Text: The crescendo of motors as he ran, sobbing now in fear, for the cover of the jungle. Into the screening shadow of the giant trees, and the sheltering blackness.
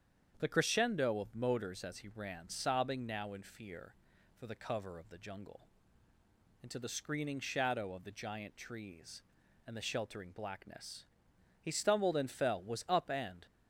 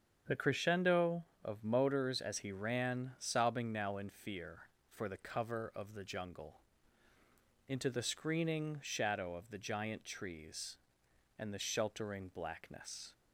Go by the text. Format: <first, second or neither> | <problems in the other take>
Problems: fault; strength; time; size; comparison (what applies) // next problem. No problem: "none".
second | starts louder than the rest; strong; until 1.4 s; 8 dB; strong in the second // goes on to say "He stumbled and fell was up and"; strong; from 11.6 s on; 1.8 s long